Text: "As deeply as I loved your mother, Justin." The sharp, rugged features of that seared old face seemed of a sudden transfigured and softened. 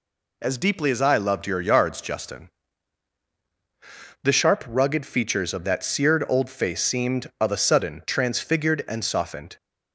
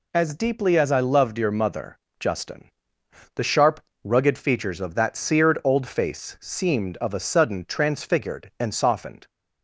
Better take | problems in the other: second | says "yards" for "mother"; at 1.6 s

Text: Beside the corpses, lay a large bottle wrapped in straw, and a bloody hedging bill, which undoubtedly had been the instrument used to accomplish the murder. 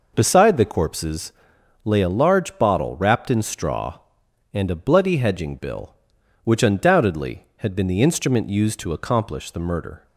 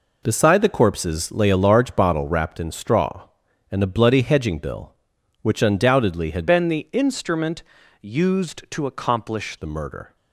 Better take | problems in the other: first | changes voice from "been" to "accomplish"; from 6.4 to 9.5 s; 3.1 s long // pauses between "instrument" and "used"; at 7.6 s; 0.38 s long

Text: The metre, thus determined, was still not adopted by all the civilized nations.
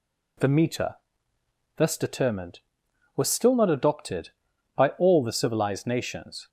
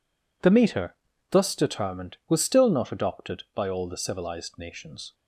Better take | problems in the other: neither | none

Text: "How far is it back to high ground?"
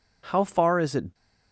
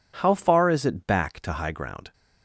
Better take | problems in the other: second | stops before "back to high ground"; at 1.1 s

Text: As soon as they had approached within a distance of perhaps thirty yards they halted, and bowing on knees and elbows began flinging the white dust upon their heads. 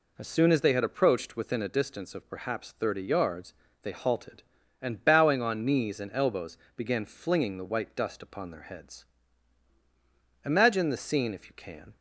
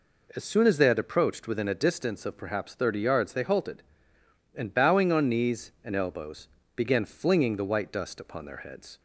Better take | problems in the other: second | pauses between "yards" and "they"; slight; at 3.5 s; 0.28 s long // pauses between "elbows" and "began"; slight; at 6.5 s; 0.18 s long; slight in the second // goes on to say "Imagine the scene if you can"; from 10.4 s on; 1.5 s long

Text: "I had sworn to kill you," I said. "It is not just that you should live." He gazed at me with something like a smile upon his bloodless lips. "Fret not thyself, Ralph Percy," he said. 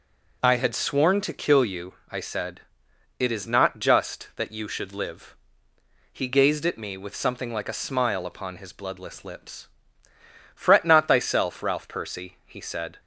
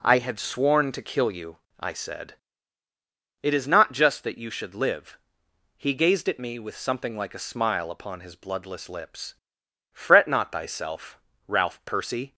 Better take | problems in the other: first | stops before "he said"; at 12.3 s

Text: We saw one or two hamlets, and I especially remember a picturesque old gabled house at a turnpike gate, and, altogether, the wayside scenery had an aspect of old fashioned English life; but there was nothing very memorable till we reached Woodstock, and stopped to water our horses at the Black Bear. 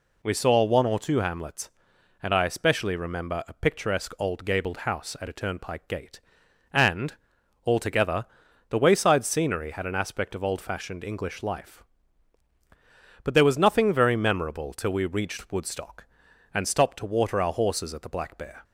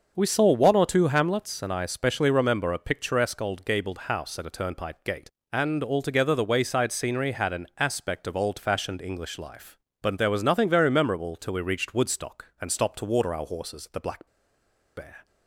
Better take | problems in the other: first | starts louder than the rest; until 1.1 s; 6.5 dB // pauses between "Black" and "Bear"; noticeable; at 14.2 s; 0.71 s long

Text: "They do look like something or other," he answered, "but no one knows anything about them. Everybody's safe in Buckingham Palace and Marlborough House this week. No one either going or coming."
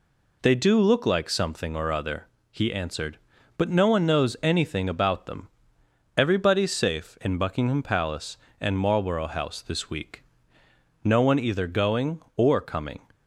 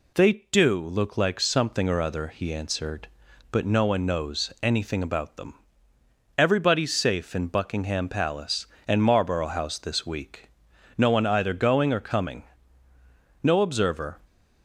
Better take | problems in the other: first | goes on to say "No observer"; noticeable; from 13.4 s on; 0.78 s long

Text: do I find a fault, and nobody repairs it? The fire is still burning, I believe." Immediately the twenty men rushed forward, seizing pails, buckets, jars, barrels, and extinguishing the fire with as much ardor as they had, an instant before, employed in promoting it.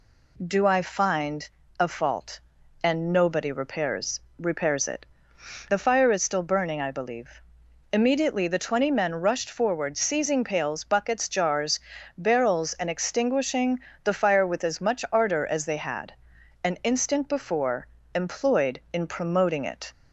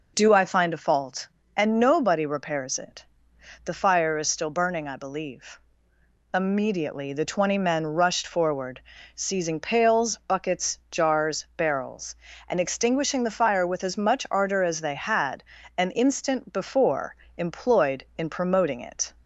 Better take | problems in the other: second | pauses between "find" and "a"; slight; at 1.4 s; 0.30 s long // says "repairs" twice; at 4.3 s // pauses between "extinguishing" and "the"; slight; at 13.7 s; 0.24 s long

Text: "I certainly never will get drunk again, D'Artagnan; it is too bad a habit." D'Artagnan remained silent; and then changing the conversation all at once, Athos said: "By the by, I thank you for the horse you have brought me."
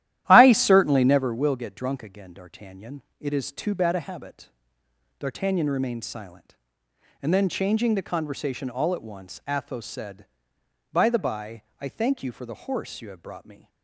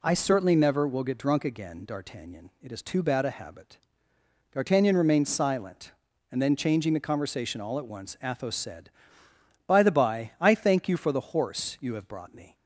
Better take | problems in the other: second | starts louder than the rest; strong; until 1.3 s; 13 dB

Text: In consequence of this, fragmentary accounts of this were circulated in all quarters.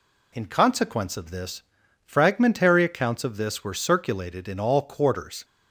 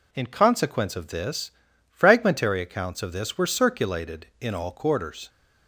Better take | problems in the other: neither | none

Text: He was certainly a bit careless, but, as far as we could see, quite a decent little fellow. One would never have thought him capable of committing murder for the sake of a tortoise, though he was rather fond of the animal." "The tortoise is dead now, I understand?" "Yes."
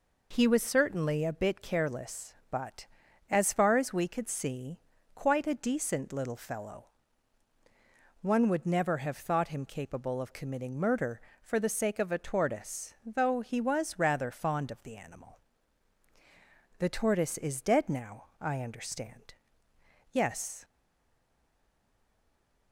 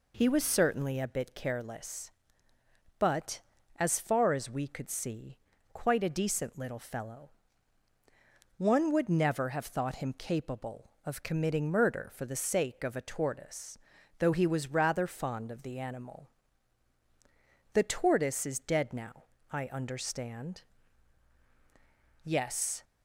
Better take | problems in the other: second | stays silent after the last word; noticeable; from 20.6 s on; 2.1 s long

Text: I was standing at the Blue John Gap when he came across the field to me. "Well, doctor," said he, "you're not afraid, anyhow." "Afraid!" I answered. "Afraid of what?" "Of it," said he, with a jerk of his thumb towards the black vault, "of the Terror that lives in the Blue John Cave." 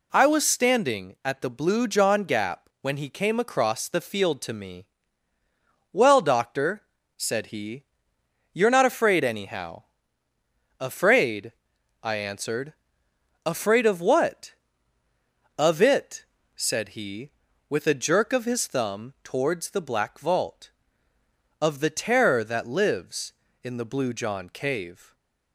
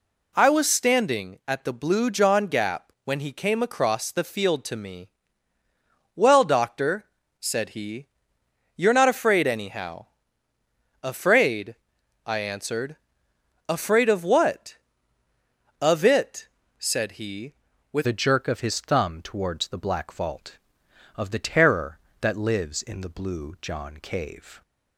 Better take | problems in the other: first | changes voice at "a"; from 18.0 s on; 6.6 s long

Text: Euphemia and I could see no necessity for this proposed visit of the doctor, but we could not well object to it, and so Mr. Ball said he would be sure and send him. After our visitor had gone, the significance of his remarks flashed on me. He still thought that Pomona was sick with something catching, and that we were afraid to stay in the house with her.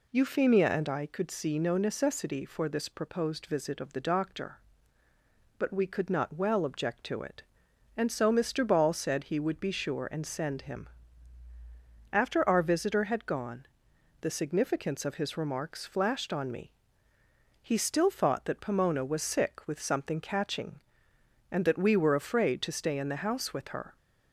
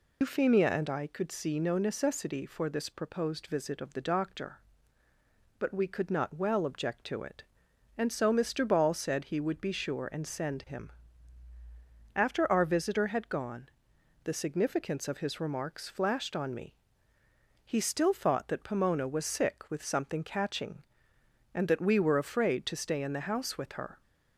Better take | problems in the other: first | loses the start of "Euphemia"; at 0.2 s; 105 ms

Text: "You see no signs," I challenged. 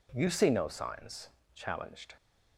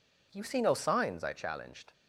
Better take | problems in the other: second | skips "I"; at 1.4 s

